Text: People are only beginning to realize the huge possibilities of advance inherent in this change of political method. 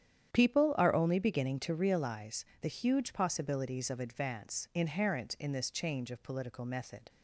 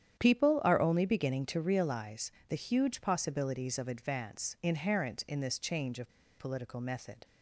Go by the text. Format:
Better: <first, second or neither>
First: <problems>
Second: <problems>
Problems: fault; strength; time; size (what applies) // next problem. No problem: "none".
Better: first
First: starts louder than the rest; strong; until 1.3 s; 9.5 dB // pauses between "realize" and "the"; slight; at 2.4 s; 0.17 s long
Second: starts louder than the rest; strong; until 1.2 s; 9.5 dB // pauses between "realize" and "the"; slight; at 2.3 s; 0.18 s long // pauses between "of" and "political"; slight; at 6.0 s; 0.28 s long